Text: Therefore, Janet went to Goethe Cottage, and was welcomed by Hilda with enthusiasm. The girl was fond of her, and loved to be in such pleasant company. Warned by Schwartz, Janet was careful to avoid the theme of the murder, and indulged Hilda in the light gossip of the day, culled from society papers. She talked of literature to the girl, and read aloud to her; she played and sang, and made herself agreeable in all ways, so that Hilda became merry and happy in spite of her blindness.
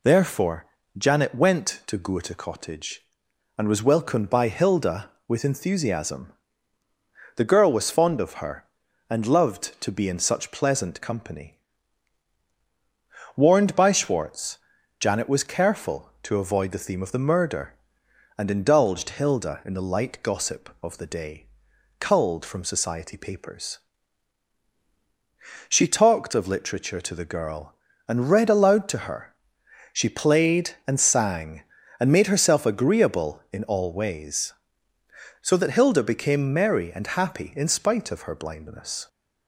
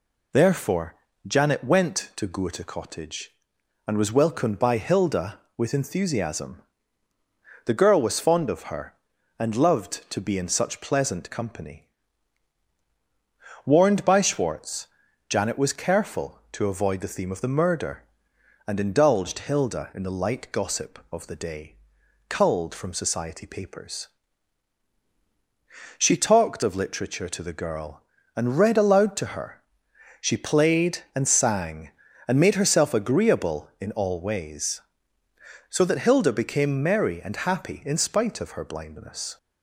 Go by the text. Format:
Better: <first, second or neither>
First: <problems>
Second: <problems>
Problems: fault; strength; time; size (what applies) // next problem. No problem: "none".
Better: neither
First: none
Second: none